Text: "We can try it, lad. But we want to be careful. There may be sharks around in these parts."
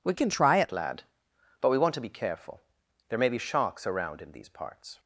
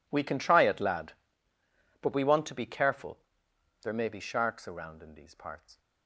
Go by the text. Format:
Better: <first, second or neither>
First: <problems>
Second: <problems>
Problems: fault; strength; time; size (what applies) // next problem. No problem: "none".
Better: second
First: changes voice from "can" to "it"; from 0.1 to 0.7 s; 0.6 s long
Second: none